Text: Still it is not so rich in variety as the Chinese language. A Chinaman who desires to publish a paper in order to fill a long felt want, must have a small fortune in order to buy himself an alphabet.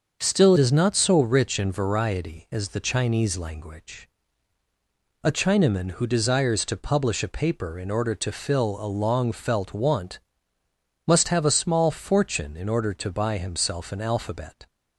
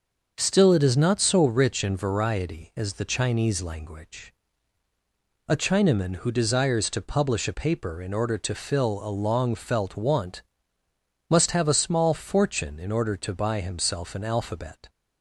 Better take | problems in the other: second | starts louder than the rest; until 1.2 s; 6.5 dB; also in the second // skips "it"; at 0.5 s

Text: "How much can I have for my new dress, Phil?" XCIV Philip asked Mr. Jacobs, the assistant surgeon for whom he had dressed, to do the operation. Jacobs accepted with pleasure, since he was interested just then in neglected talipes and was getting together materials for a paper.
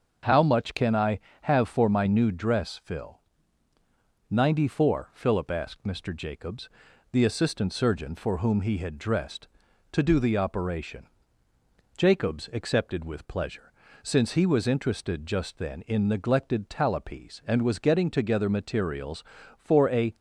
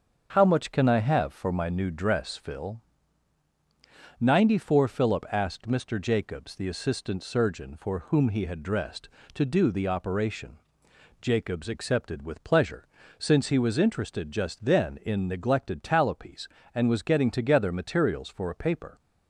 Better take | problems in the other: second | starts louder than the rest; until 1.4 s; 6.5 dB; also in the second // stops before "paper"; at 20.1 s

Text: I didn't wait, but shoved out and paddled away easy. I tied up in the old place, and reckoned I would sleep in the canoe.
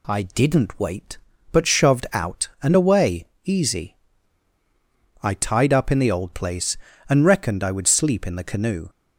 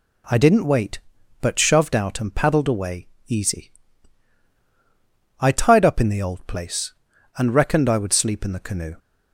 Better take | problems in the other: second | skips "paddled"; at 2.7 s // pauses between "away" and "easy"; slight; at 3.2 s; 0.18 s long; slight in the second

